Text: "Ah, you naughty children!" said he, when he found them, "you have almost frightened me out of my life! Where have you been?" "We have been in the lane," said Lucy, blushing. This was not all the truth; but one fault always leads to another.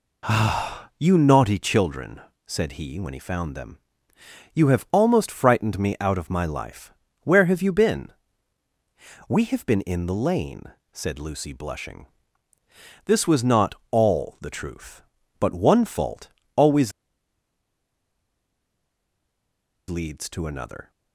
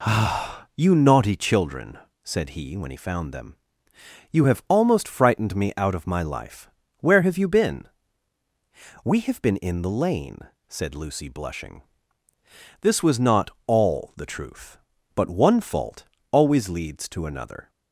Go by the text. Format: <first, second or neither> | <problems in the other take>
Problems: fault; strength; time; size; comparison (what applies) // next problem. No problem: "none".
second | pauses between "not" and "all"; slight; at 13.7 s; 0.16 s long; slight in the second // pauses between "fault" and "always"; slight; at 16.2 s; 0.26 s long; slight in the second // pauses between "always" and "leads"; strong; at 16.9 s; 2.9 s long